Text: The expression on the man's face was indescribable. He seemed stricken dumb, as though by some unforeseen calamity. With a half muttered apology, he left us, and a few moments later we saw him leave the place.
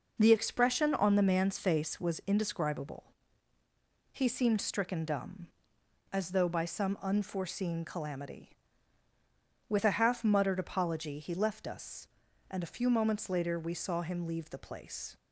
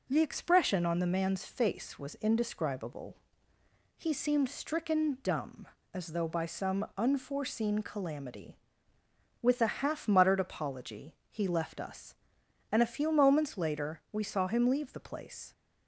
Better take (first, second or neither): neither